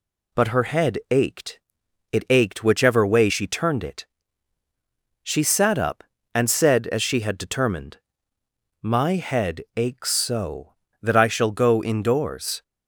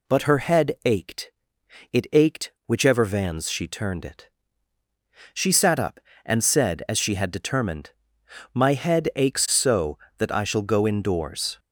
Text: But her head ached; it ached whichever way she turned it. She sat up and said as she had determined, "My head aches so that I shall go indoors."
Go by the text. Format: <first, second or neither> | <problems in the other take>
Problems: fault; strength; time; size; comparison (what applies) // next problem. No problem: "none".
first | says "vans" for "way"; at 3.0 s